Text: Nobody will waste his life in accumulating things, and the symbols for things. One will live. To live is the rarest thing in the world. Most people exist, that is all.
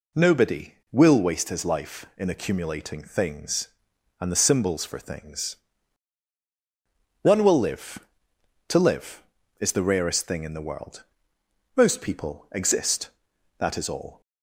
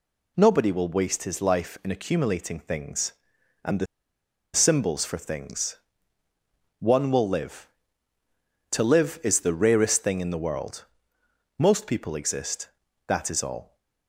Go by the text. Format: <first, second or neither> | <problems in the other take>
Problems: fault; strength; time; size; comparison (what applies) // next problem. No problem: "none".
first | pauses between "the" and "symbols"; noticeable; at 3.8 s; 0.68 s long